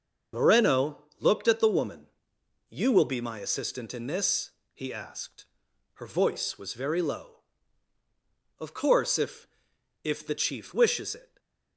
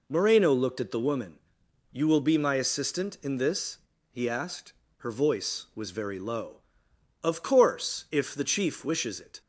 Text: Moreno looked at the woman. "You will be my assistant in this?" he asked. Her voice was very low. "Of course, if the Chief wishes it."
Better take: second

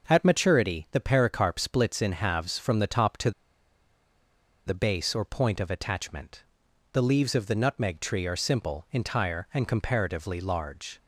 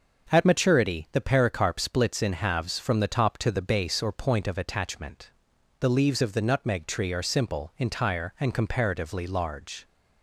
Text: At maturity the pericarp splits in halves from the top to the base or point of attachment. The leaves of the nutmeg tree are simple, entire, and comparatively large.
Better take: second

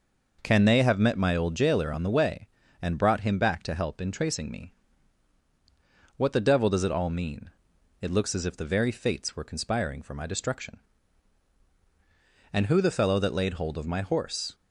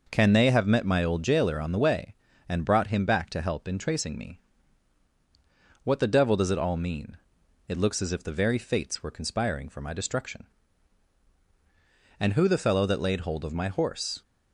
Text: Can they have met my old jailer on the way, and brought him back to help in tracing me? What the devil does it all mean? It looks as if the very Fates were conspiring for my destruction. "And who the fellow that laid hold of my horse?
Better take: neither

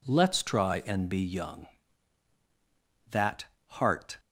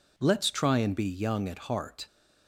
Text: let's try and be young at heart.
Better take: second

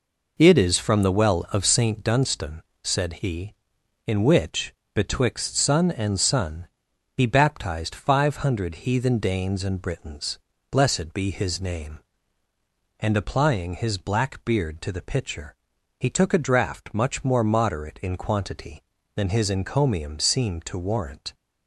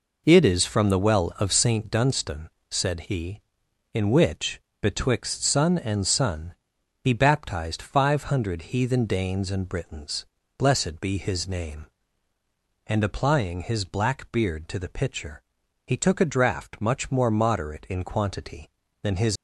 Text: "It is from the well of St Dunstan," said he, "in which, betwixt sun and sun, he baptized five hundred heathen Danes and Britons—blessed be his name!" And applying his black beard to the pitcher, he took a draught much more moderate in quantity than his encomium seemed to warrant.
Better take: first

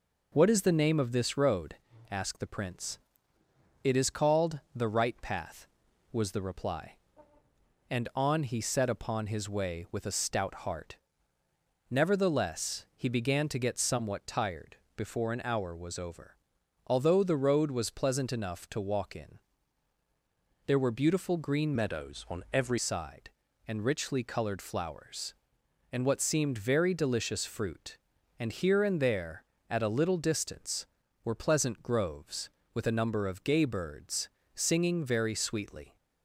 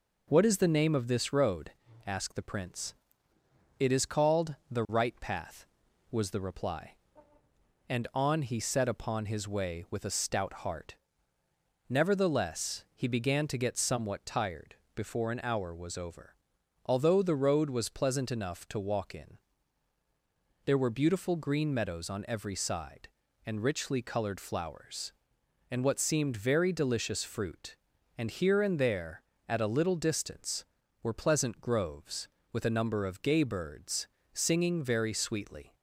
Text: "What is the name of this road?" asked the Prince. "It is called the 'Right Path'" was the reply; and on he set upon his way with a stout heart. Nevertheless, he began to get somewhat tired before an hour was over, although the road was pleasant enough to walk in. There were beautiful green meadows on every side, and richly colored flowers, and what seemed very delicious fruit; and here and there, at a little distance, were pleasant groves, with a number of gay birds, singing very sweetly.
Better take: second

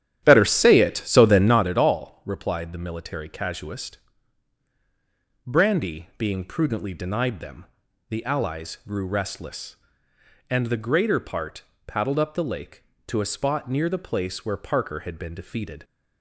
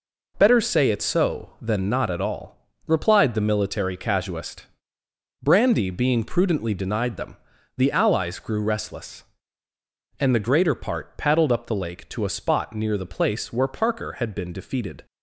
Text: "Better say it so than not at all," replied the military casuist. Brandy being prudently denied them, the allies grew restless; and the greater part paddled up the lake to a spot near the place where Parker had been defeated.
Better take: second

